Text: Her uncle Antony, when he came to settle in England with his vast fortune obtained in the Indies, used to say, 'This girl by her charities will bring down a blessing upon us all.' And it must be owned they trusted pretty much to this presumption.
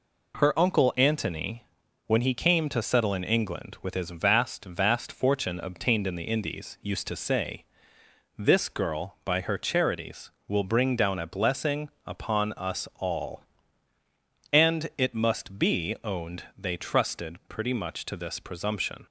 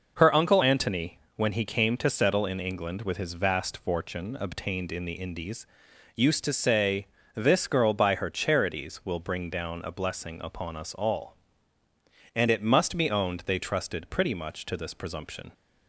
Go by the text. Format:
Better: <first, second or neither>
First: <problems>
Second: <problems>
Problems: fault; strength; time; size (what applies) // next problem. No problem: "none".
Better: second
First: says "vast" twice; at 4.6 s // pauses between "blessing" and "upon"; slight; at 11.8 s; 0.18 s long // pauses between "owned" and "they"; slight; at 16.4 s; 0.16 s long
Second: none